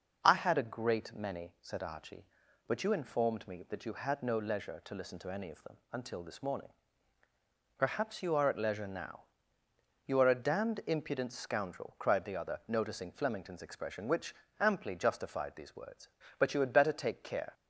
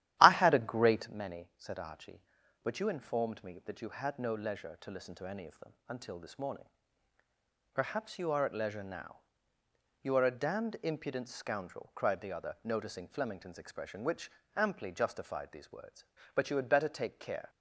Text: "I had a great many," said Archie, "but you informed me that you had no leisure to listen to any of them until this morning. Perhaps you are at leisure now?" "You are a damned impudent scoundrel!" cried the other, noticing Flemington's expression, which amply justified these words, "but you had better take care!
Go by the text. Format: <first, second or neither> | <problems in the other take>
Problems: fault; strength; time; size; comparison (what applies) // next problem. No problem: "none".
first | starts louder than the rest; strong; until 1.2 s; 13 dB // pauses between "them" and "until"; slight; at 5.7 s; 0.16 s long; slight in the first // pauses between "which" and "amply"; slight; at 14.3 s; 0.24 s long; slight in the first